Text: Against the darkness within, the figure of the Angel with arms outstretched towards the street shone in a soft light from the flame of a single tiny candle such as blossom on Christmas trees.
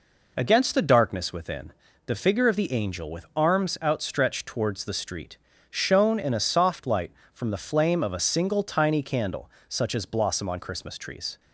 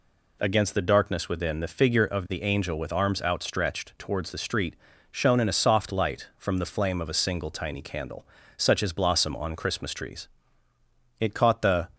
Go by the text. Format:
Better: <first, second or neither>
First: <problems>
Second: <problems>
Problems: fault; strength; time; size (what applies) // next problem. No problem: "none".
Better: first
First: pauses between "street" and "shone"; slight; at 5.3 s; 0.34 s long // pauses between "candle" and "such"; slight; at 9.4 s; 0.18 s long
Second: pauses between "street" and "shone"; slight; at 4.7 s; 0.36 s long // pauses between "candle" and "such"; slight; at 8.2 s; 0.32 s long // goes on to say "It caught the"; noticeable; from 11.1 s on; 0.72 s long